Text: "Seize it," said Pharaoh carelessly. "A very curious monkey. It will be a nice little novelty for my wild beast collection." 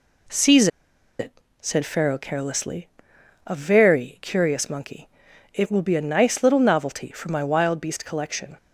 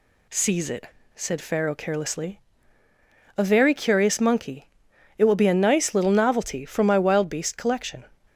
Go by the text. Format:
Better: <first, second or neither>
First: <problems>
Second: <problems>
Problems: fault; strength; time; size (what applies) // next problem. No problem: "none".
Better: second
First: pauses between "Seize" and "it"; noticeable; at 0.6 s; 0.51 s long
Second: none